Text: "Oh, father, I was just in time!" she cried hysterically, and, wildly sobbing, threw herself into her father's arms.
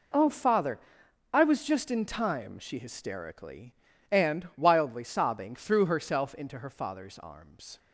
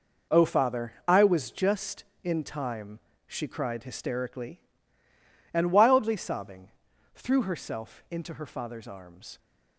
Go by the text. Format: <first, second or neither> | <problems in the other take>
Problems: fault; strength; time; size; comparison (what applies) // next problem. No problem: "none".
second | skips "cried"; at 2.7 s